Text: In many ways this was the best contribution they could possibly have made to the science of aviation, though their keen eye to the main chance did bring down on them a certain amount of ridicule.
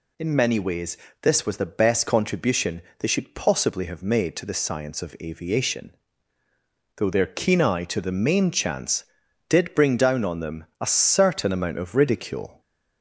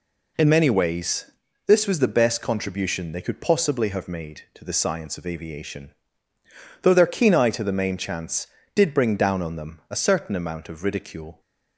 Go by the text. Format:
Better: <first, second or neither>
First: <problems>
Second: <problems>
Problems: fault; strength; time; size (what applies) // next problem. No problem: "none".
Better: second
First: pauses between "ways" and "this"; slight; at 0.9 s; 0.26 s long // pauses between "contribution" and "they"; slight; at 2.8 s; 0.18 s long // says "should" for "could"; at 3.0 s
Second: pauses between "ways" and "this"; slight; at 1.3 s; 0.36 s long